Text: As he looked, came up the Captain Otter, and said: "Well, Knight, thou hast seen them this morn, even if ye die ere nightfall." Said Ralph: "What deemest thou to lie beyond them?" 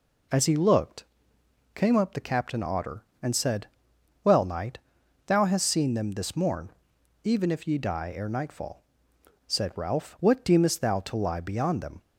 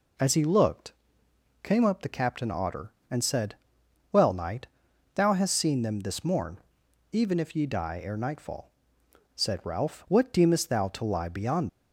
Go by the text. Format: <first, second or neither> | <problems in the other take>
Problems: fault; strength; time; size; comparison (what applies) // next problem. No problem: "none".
first | stops before "them"; at 11.6 s